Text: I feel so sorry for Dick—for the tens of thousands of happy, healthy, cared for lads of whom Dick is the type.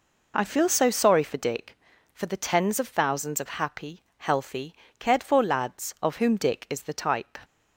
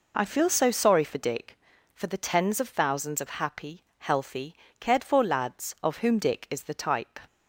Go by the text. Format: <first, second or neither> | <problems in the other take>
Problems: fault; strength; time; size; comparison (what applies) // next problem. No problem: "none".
neither | none